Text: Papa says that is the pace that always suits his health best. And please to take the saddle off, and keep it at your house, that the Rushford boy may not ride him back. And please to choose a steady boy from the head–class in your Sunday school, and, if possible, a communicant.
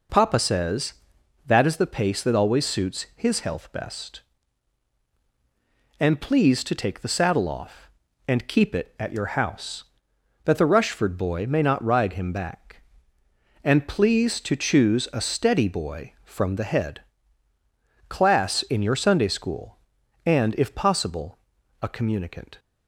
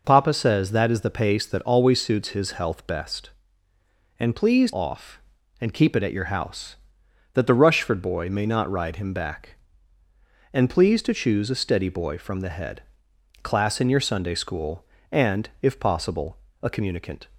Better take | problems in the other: first | skips "to take the saddle"; at 4.7 s

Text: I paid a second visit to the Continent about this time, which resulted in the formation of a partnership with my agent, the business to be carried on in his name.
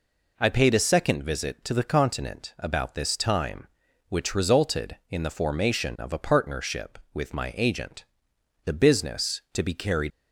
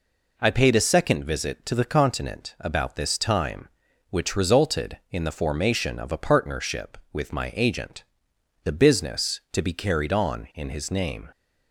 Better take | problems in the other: second | stops before "on in his name"; at 10.1 s

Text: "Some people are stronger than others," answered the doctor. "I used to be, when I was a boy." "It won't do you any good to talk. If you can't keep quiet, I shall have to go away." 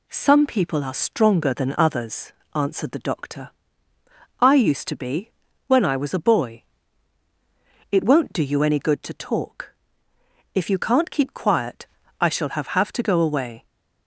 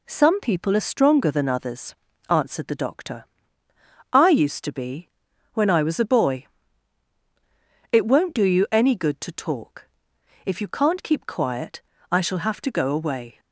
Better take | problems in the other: second | says "have" twice; at 12.7 s

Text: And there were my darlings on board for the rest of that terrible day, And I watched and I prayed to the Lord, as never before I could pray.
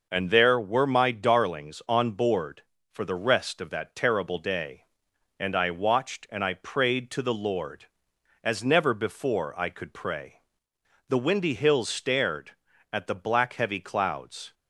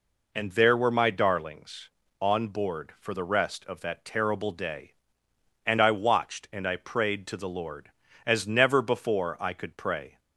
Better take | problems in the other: second | goes on to say "The windy hills stared at the black heavy clouds"; strong; from 11.0 s on; 3.4 s long

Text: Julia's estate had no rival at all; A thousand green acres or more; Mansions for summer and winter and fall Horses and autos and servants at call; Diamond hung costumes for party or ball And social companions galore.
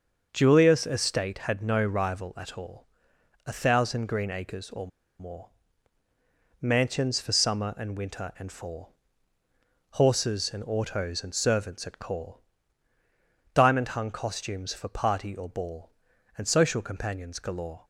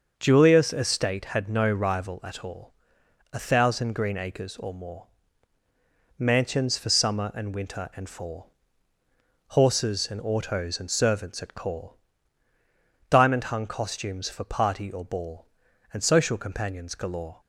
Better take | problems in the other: second | starts louder than the rest; until 1.3 s; 6 dB; also in the second // pauses between "or" and "more"; slight; at 4.8 s; 0.32 s long // pauses between "fall" and "Horses"; noticeable; at 8.9 s; 0.98 s long; noticeable in the second

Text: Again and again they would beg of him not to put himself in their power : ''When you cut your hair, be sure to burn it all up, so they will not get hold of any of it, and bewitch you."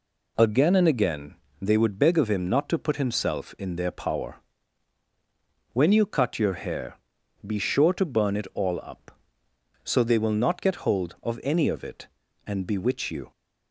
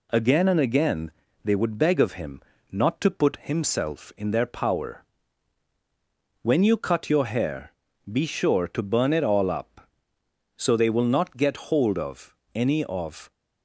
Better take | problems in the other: first | pauses between "again" and "they"; slight; at 1.1 s; 0.32 s long; slight in the first // pauses between "him" and "not"; slight; at 2.4 s; 0.30 s long // pauses between "of" and "any"; slight; at 12.3 s; 0.18 s long // stops before "it and bewitch you"; at 13.3 s

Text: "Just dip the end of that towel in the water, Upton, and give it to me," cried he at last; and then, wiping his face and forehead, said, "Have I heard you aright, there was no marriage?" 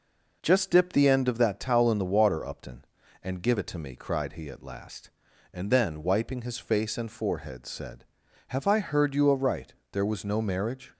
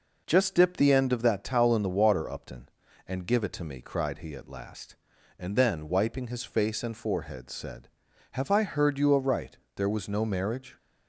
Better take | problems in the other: neither | none

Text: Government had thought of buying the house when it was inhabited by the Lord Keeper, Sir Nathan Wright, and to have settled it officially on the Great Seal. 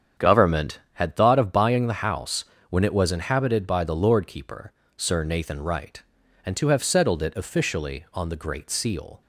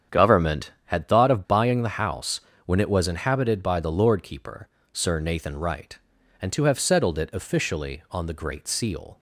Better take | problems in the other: neither | starts louder than the rest; strong; the same in both // pauses between "house" and "when"; slight; the same in both

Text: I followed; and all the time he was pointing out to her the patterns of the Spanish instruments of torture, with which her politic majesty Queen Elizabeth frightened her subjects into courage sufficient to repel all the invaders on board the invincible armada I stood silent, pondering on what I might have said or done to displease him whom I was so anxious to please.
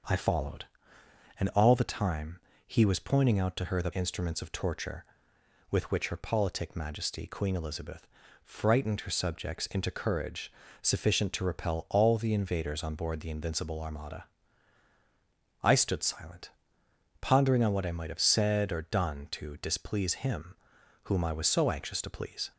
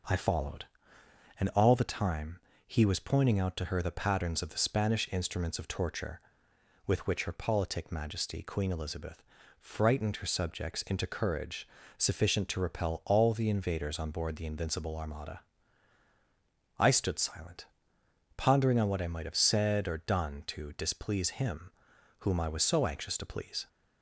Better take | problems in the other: second | starts louder than the rest; until 1.8 s; 6 dB // pauses between "time" and "he"; slight; at 2.3 s; 0.28 s long; slight in the second // skips "patterns of the Spanish"; at 3.9 s // pauses between "Elizabeth" and "frightened"; at 8.0 s; 0.38 s long; also in the second // pauses between "courage" and "sufficient"; slight; at 10.4 s; 0.30 s long; slight in the second // pauses between "armada" and "I"; strong; at 14.2 s; 1.3 s long; strong in the second // pauses between "him" and "whom"; noticeable; at 20.5 s; 0.48 s long; noticeable in the second

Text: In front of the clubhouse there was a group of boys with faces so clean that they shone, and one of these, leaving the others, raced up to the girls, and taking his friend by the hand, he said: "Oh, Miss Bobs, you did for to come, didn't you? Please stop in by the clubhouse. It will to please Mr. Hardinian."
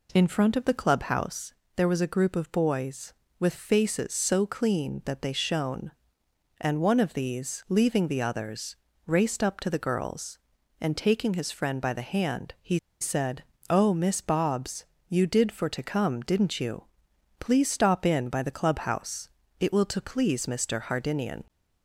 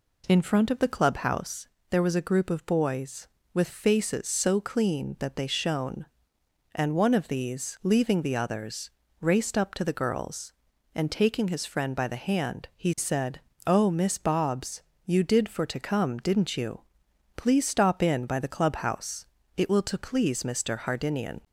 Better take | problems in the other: second | pauses between "clubhouse" and "there"; slight; at 1.5 s; 0.24 s long; slight in the second // pauses between "he" and "said"; slight; at 12.7 s; 0.24 s long

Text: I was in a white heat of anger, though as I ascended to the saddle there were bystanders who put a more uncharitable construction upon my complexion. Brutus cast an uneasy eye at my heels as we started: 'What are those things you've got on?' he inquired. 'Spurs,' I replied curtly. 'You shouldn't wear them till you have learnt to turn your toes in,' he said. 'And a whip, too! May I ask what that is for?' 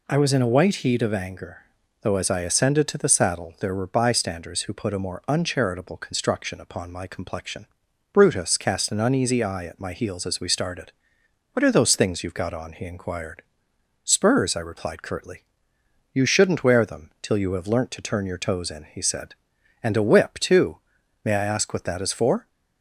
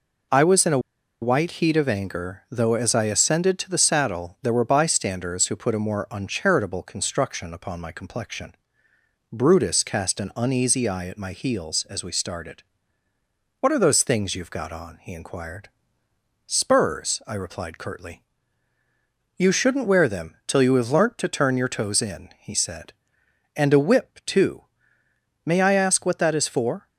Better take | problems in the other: first | pauses between "a" and "white"; at 0.7 s; 0.42 s long

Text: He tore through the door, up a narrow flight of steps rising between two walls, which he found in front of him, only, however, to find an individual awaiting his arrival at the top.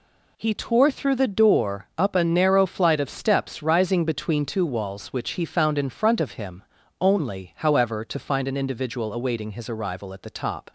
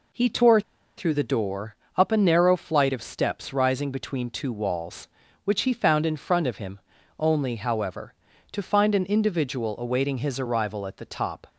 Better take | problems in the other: first | pauses between "tore" and "through"; at 0.5 s; 0.36 s long

